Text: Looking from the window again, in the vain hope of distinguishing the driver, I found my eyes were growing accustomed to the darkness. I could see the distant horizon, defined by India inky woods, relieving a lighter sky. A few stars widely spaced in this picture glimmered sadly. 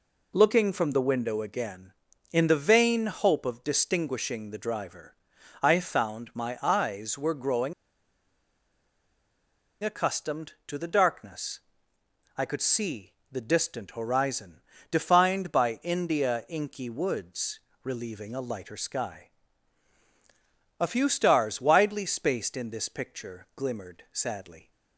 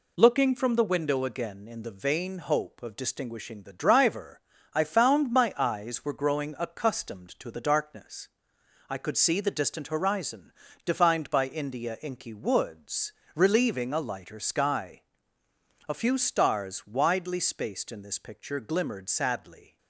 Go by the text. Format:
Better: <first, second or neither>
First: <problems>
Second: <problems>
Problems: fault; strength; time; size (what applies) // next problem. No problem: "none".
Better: second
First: pauses between "growing" and "accustomed"; strong; at 7.7 s; 2.1 s long // pauses between "see" and "the"; slight; at 13.1 s; 0.18 s long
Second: none